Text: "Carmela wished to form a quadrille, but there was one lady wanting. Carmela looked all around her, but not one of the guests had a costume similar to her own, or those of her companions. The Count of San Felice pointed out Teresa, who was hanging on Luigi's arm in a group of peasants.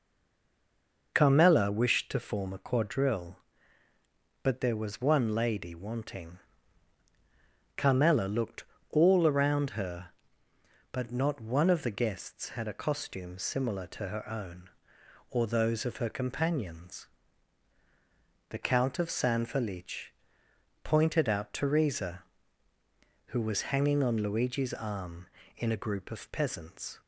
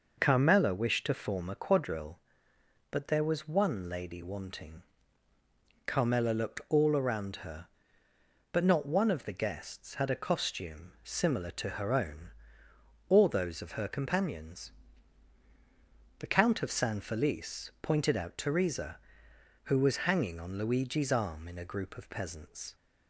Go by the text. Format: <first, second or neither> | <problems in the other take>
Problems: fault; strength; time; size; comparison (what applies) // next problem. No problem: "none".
second | stays silent before the first word; until 1.1 s; 1.1 s long // pauses between "looked" and "all"; slight; at 8.6 s; 0.24 s long // pauses between "Felice" and "pointed"; noticeable; at 20.0 s; 0.74 s long